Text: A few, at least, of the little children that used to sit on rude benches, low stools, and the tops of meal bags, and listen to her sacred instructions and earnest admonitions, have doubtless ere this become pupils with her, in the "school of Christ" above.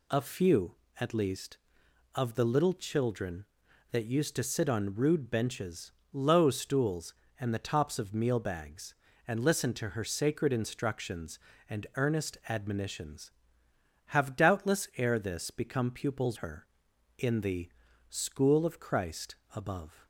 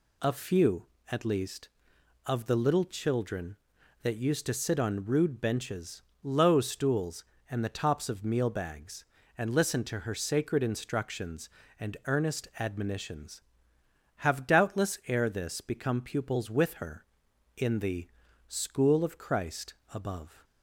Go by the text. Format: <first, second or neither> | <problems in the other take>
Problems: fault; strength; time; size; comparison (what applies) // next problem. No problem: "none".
second | skips "with"; at 16.3 s // pauses between "the" and "school"; at 17.6 s; 0.40 s long; also in the second // pauses between "Christ" and "above"; slight; at 19.3 s; 0.20 s long; slight in the second